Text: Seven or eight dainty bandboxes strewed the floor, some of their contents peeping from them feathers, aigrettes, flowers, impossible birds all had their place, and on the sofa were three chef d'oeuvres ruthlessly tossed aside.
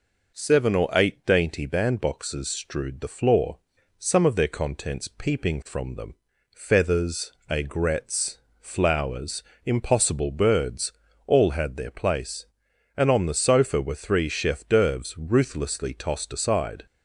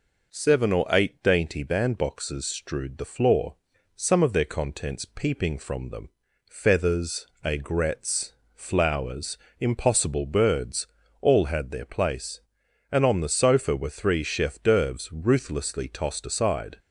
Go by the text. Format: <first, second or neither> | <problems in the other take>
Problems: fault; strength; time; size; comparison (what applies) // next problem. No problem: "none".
neither | pauses between "them" and "feathers"; the same in both // pauses between "birds" and "all"; slight; the same in both